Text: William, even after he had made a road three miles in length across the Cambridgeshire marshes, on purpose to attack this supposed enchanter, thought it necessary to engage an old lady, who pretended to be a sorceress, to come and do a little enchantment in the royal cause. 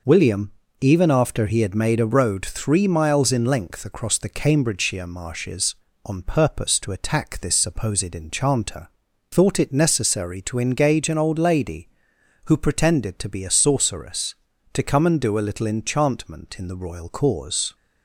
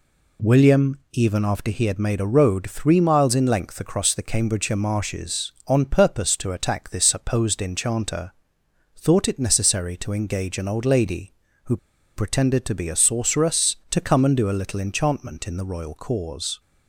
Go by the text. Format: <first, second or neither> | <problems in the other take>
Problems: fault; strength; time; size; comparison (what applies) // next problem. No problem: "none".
first | pauses between "who" and "pretended"; at 11.7 s; 0.39 s long